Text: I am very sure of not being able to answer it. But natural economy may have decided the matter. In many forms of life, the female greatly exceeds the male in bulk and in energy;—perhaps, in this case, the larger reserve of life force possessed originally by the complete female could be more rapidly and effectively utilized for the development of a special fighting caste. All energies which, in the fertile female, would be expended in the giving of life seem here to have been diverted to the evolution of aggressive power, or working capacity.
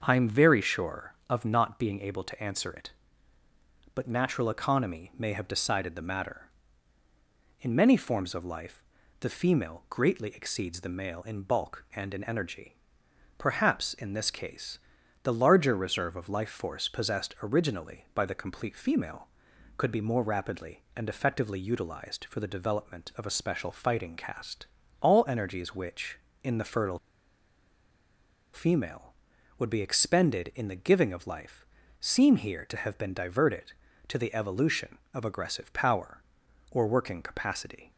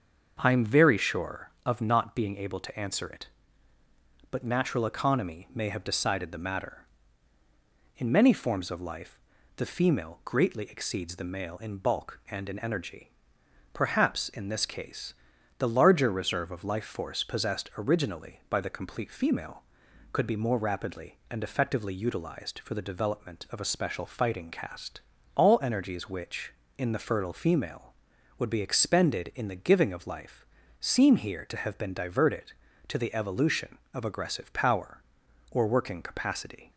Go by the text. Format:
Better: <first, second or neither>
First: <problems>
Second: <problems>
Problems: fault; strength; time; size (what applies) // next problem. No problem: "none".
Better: second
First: starts louder than the rest; until 1.0 s; 6.5 dB // pauses between "fertile" and "female"; strong; at 26.9 s; 1.5 s long // pauses between "life" and "seem"; slight; at 31.6 s; 0.34 s long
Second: starts louder than the rest; until 1.4 s; 6.5 dB // pauses between "life" and "seem"; slight; at 30.4 s; 0.34 s long